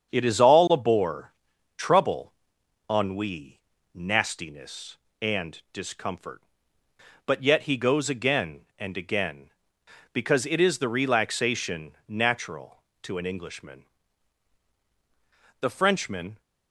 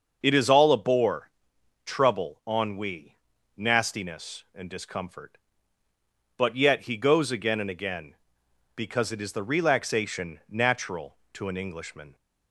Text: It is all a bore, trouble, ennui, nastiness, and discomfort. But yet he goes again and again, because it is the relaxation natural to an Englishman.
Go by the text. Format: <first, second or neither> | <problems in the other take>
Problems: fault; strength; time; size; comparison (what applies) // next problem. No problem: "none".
second | starts louder than the rest; until 1.1 s; 7 dB; also in the second // pauses between "relaxation" and "natural"; slight; at 11.9 s; 0.16 s long // goes on to say "The Frenchman"; noticeable; from 15.6 s on; 0.80 s long